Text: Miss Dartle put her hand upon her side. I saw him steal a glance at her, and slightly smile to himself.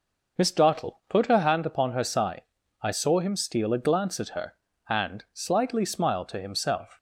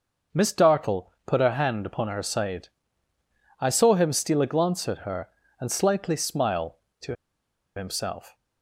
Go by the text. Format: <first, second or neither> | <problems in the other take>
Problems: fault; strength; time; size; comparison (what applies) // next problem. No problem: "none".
first | pauses between "to" and "himself"; noticeable; at 7.1 s; 0.61 s long